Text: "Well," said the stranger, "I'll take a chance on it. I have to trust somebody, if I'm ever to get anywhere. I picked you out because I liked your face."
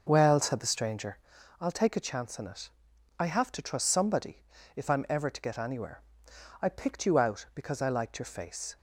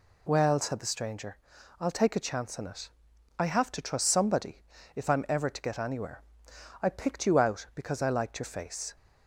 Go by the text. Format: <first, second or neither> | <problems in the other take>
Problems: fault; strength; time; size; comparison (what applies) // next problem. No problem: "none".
second | starts louder than the rest; noticeable; until 1.4 s; 6 dB